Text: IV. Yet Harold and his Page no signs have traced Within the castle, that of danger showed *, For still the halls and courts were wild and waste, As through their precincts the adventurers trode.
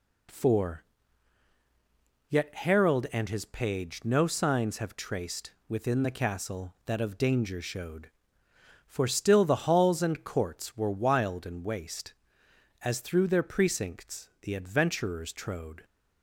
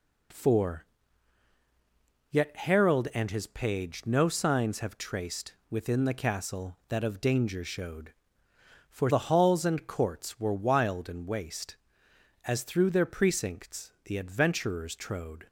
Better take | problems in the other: first | skips "still"; at 9.0 s

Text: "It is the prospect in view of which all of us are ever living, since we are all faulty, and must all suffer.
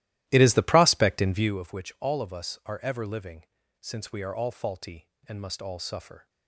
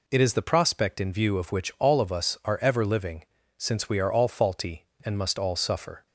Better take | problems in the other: second | starts louder than the rest; strong; until 1.6 s; 14.5 dB

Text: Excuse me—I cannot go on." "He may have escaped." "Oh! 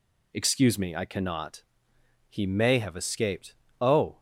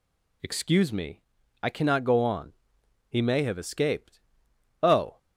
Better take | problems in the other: second | skips "go on"; at 1.9 s

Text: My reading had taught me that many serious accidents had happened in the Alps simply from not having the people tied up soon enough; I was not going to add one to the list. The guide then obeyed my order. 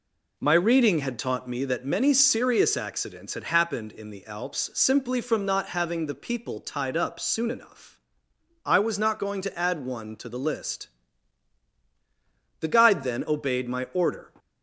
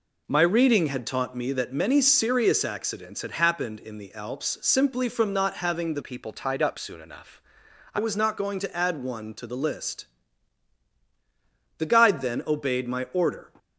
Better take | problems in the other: first | changes voice from "people" to "I"; from 6.0 to 7.9 s; 1.9 s long

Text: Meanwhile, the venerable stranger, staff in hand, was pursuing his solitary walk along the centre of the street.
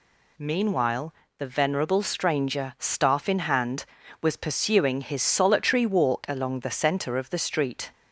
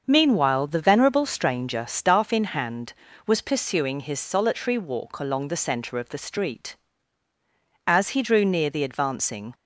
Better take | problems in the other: first | starts louder than the rest; until 1.0 s; 6.5 dB // goes on to say "As he drew near the advancing"; from 7.8 s on; 1.6 s long

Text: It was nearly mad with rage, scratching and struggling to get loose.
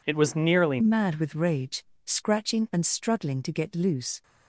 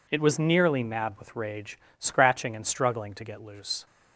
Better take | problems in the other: second | changes voice at "mad"; from 0.8 s on; 3.4 s long

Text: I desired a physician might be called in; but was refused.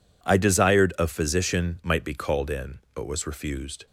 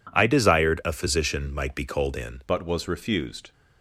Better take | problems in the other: first | changes voice at "but"; from 2.4 s on; 1.1 s long

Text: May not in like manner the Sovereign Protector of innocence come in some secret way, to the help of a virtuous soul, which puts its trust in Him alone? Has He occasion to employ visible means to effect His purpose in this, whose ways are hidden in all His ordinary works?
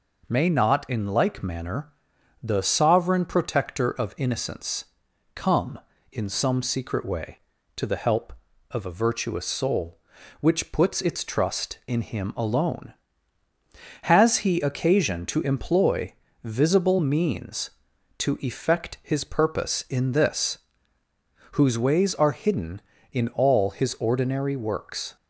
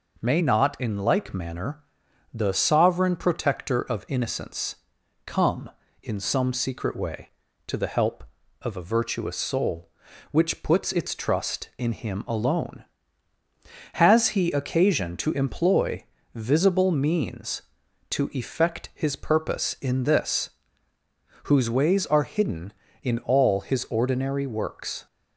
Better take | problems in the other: neither | pauses between "manner" and "the"; noticeable; the same in both // pauses between "innocence" and "come"; noticeable; the same in both // pauses between "employ" and "visible"; slight; the same in both

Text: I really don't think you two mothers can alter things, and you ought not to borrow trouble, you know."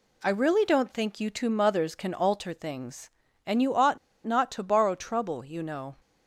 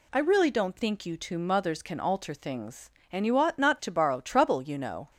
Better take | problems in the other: second | pauses between "ought" and "not"; slight; at 3.9 s; 0.27 s long

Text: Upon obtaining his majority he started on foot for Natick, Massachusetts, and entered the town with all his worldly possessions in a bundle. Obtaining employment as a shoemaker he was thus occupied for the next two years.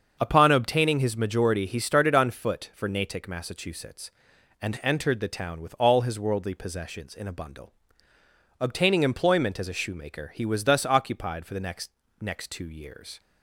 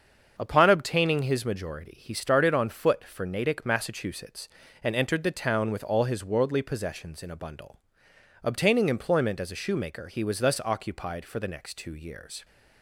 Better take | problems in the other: second | starts louder than the rest; until 1.2 s; 7 dB; also in the second // says "next" twice; at 12.1 s

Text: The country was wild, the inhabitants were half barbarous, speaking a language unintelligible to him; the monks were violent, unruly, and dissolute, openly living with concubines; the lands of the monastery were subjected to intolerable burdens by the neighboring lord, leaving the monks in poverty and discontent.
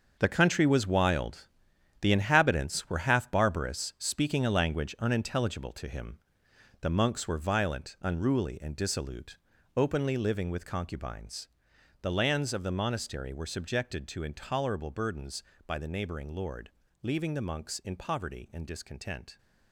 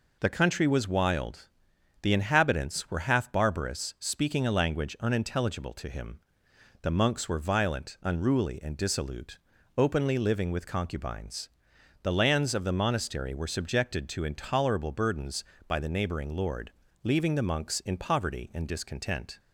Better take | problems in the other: second | gets quieter; strong; throughout; 11 dB

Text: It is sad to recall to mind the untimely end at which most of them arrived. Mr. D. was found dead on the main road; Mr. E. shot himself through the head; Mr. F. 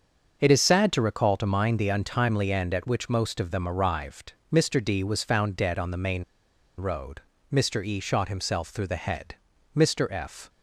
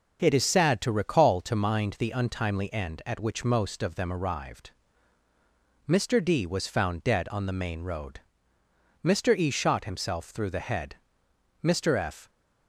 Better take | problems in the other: second | starts louder than the rest; until 1.4 s; 6.5 dB // pauses between "main" and "road"; noticeable; at 6.2 s; 0.55 s long

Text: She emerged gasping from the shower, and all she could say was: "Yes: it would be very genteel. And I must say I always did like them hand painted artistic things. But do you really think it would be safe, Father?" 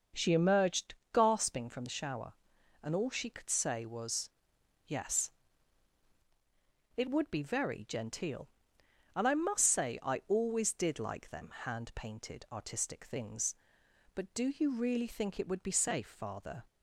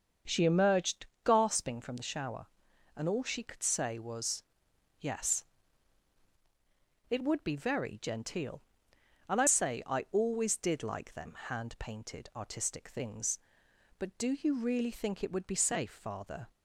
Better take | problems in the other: first | starts louder than the rest; until 1.4 s; 7 dB; also in the first // pauses between "emerged" and "gasping"; slight; at 1.0 s; 0.18 s long; slight in the first // skips "must"; at 9.4 s

